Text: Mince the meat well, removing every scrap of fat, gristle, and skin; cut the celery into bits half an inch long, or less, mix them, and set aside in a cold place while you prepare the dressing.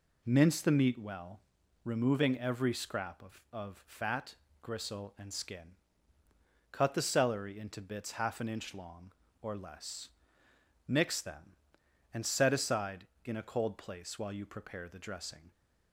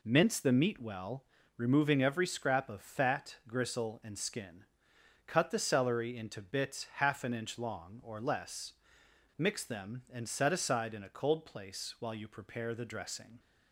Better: second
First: says "of" twice; at 3.5 s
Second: none

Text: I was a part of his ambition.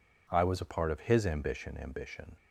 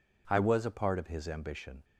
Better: second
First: says "ambition" twice; at 1.8 s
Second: none

